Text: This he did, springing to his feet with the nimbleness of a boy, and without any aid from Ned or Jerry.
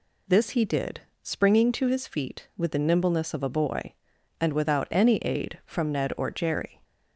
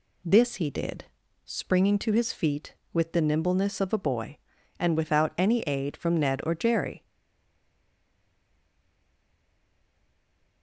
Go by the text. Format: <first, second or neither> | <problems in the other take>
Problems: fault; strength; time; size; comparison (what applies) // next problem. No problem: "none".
first | stays silent after the last word; strong; from 7.0 s on; 3.6 s long